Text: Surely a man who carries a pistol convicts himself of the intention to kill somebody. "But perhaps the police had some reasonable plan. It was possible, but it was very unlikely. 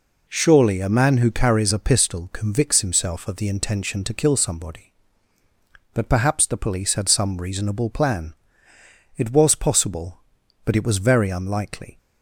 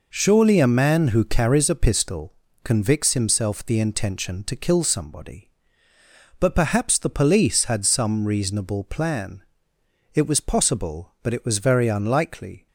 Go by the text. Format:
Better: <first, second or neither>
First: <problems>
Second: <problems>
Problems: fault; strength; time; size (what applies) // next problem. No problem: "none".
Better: first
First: none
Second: pauses between "pistol" and "convicts"; slight; at 2.3 s; 0.32 s long // skips "of"; at 3.6 s